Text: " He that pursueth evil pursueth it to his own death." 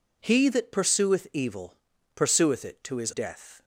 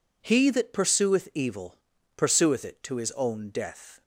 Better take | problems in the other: second | pauses between "evil" and "pursueth"; slight; at 1.7 s; 0.36 s long; slight in the second // skips "own"; at 3.1 s

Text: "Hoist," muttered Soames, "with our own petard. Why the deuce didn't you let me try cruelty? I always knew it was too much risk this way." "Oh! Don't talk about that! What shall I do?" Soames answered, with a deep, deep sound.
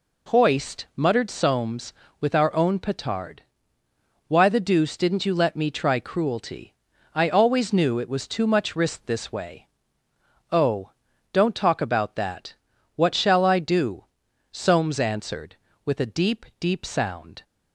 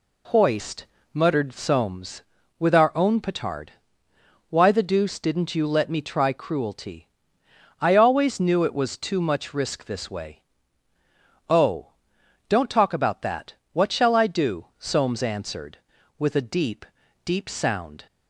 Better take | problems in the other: neither | none

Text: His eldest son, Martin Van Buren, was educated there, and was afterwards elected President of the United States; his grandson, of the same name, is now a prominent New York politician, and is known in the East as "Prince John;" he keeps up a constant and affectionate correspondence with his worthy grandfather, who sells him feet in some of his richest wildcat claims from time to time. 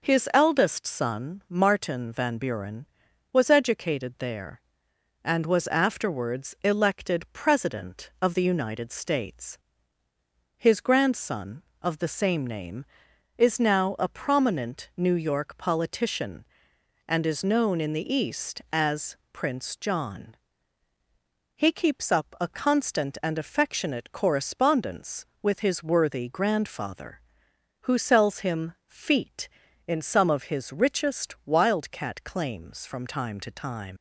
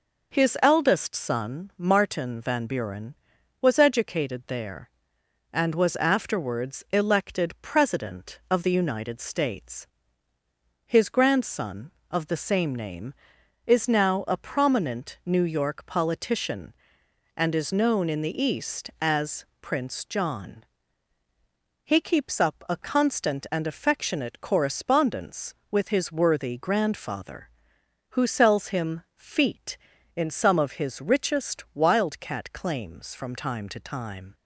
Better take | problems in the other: second | pauses between "as" and "Prince"; slight; at 19.1 s; 0.16 s long; slight in the second // leaves "time" unfinished; at 33.9 s; 90 ms

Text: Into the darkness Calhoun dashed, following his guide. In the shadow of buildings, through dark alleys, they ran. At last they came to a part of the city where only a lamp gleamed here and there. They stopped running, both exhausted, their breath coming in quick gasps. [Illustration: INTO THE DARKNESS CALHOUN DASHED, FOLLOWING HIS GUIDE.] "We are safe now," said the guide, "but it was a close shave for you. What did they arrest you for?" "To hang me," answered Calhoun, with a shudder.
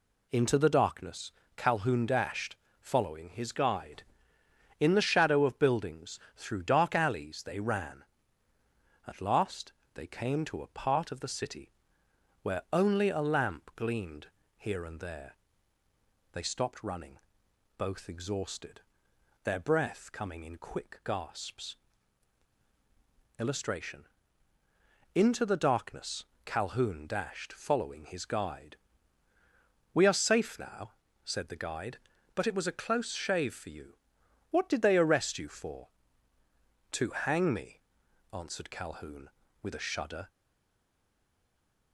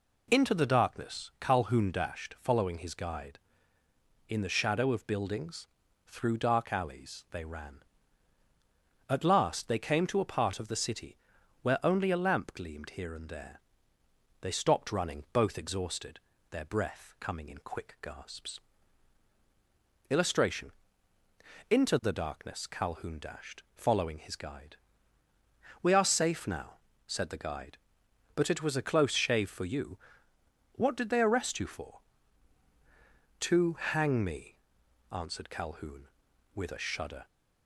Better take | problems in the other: second | pauses between "darkness" and "Calhoun"; slight; at 1.3 s; 0.24 s long // pauses between "last" and "they"; slight; at 9.7 s; 0.22 s long // pauses between "city" and "where"; noticeable; at 11.7 s; 0.74 s long; noticeable in the second // pauses between "gleamed" and "here"; slight; at 14.2 s; 0.28 s long // pauses between "DARKNESS" and "CALHOUN"; slight; at 26.2 s; 0.22 s long // stays silent after the last word; noticeable; from 40.2 s on; 1.7 s long

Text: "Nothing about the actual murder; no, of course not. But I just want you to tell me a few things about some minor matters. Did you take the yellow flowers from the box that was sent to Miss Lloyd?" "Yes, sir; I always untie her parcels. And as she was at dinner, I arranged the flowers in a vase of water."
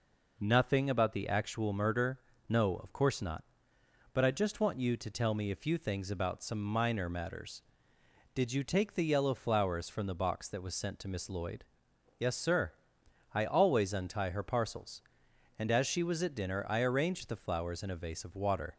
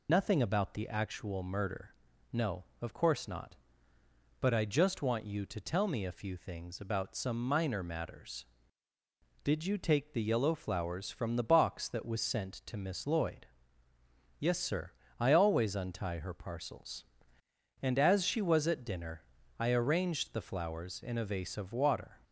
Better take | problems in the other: first | loses the start of "Nothing"; at 0.0 s; 125 ms

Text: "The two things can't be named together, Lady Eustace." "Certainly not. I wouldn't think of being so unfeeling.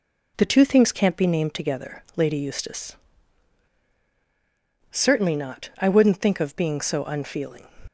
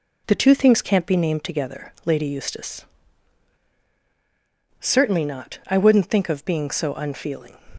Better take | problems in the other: neither | none

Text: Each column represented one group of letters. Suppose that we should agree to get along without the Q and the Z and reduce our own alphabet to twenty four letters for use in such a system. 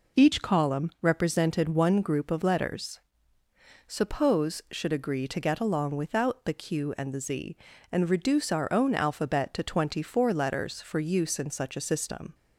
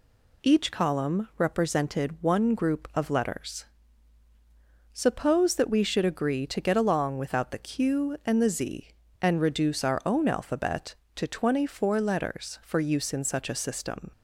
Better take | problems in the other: second | skips "that we"; at 4.6 s

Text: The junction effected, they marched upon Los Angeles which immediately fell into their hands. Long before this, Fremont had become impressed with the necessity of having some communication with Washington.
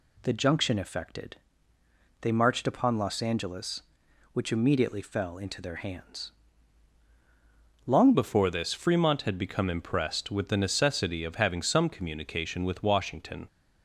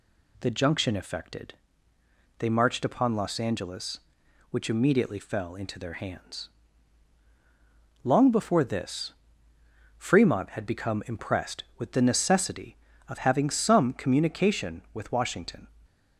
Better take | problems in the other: second | changes voice at "before"; from 8.1 s on; 5.3 s long

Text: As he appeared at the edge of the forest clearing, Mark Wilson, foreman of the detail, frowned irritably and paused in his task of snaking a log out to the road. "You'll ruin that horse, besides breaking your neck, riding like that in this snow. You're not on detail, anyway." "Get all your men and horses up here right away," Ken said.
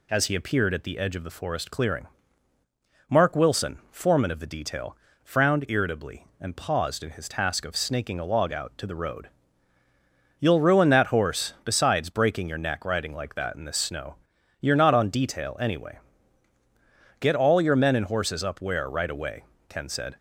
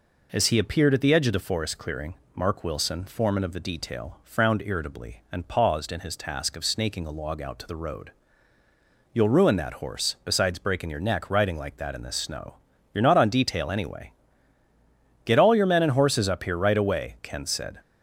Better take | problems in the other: second | says "where" for "here"; at 18.6 s

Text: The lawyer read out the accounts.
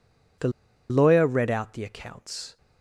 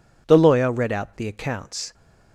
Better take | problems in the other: second | pauses between "The" and "lawyer"; at 0.4 s; 0.40 s long

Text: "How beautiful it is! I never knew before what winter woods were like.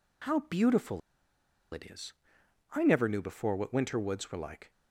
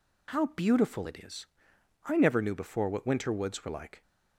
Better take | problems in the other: second | pauses between "beautiful" and "it"; noticeable; at 1.0 s; 0.73 s long

